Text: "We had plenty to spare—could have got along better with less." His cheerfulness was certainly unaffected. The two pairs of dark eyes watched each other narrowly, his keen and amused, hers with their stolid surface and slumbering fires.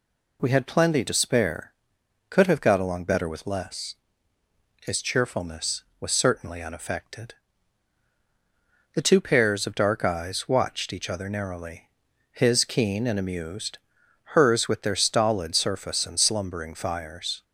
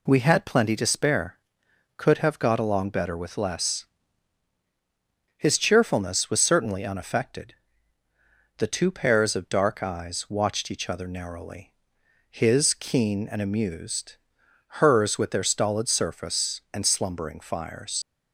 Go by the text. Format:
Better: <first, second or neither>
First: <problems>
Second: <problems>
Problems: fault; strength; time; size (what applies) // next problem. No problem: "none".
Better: first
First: none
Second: leaves "fires" unfinished; at 18.0 s; 85 ms